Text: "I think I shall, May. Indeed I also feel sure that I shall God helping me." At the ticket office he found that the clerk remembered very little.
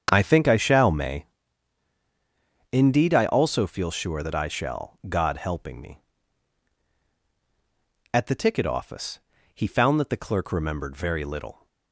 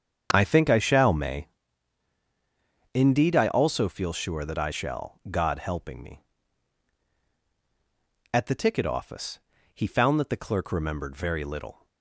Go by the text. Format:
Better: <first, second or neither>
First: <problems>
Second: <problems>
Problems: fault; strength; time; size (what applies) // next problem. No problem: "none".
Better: neither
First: starts louder than the rest; strong; until 1.1 s; 7.5 dB // pauses between "office" and "he"; slight; at 9.1 s; 0.34 s long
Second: starts louder than the rest; strong; until 1.3 s; 7.5 dB // pauses between "office" and "he"; slight; at 9.3 s; 0.34 s long